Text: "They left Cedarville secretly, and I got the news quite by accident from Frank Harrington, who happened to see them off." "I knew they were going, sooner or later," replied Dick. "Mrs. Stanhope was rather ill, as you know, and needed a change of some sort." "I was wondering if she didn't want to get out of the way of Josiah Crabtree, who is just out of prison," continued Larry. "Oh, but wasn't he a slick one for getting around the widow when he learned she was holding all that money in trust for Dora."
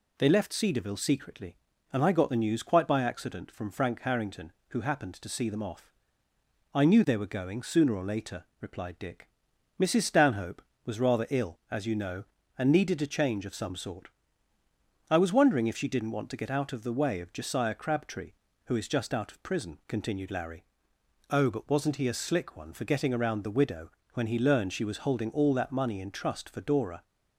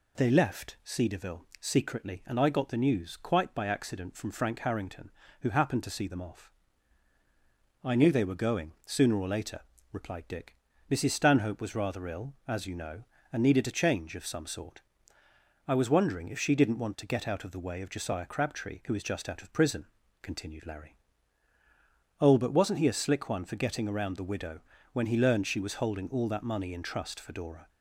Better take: neither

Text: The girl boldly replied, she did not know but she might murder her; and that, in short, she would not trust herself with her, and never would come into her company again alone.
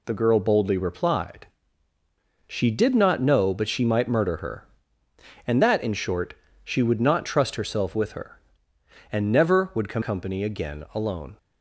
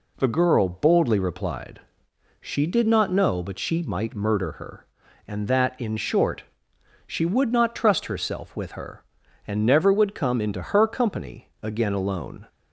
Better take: second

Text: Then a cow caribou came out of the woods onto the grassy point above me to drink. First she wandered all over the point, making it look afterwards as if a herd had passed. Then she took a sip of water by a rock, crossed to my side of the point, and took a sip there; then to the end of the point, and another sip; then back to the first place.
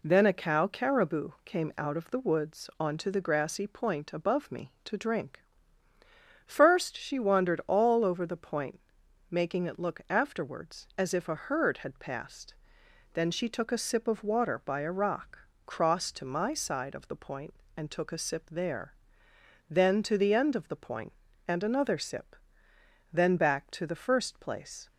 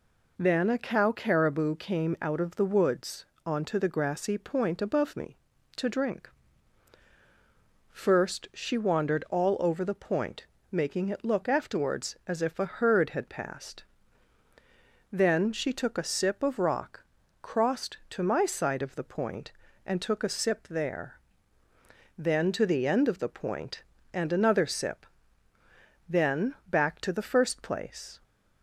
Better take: first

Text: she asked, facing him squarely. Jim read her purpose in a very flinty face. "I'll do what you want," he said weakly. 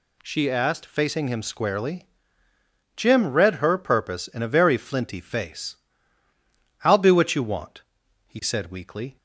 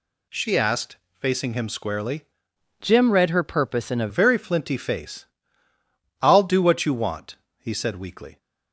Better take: first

